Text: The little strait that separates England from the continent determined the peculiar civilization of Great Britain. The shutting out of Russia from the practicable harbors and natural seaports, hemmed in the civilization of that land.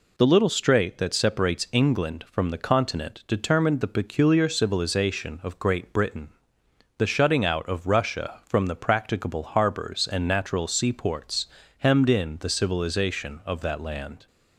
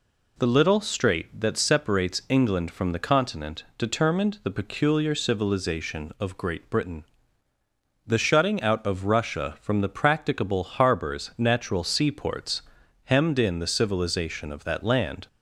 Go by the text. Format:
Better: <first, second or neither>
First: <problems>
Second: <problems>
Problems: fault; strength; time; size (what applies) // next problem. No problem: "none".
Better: first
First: none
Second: pauses between "continent" and "determined"; slight; at 3.6 s; 0.16 s long // skips "and"; at 11.3 s